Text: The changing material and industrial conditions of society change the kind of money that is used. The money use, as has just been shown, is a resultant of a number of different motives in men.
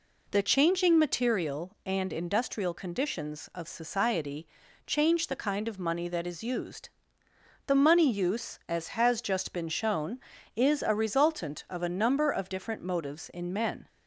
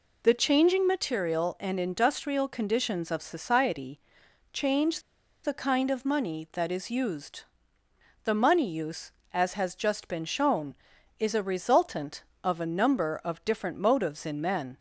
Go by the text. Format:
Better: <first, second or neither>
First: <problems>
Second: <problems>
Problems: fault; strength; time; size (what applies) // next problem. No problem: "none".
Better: first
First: pauses between "society" and "change"; at 4.4 s; 0.40 s long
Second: pauses between "society" and "change"; noticeable; at 3.9 s; 0.52 s long // pauses between "change" and "the"; at 4.9 s; 0.44 s long